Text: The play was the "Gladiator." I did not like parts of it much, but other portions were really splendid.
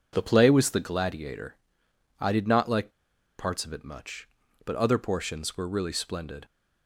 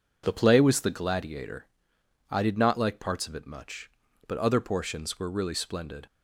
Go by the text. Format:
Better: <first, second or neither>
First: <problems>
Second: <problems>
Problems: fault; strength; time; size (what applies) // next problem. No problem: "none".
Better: second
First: pauses between "like" and "parts"; noticeable; at 2.9 s; 0.47 s long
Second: none